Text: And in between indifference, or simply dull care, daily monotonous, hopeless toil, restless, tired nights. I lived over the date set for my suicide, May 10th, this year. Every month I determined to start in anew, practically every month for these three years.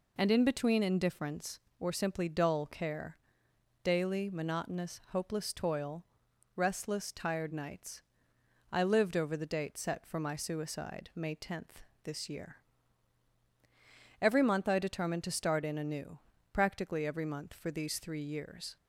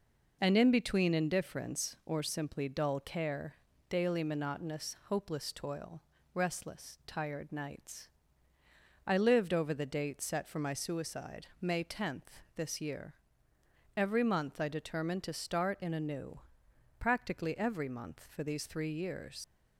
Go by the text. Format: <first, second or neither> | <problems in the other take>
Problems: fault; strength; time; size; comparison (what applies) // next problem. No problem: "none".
first | leaves "years" unfinished; at 19.4 s; 85 ms